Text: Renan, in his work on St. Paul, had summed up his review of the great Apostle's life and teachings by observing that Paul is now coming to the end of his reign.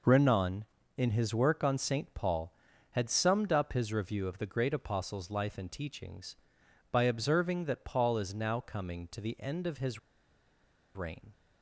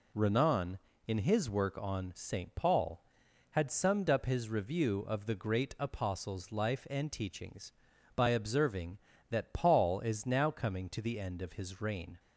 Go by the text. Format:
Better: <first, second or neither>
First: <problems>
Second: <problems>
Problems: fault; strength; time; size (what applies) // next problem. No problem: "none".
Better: second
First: pauses between "his" and "reign"; noticeable; at 9.9 s; 0.96 s long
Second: none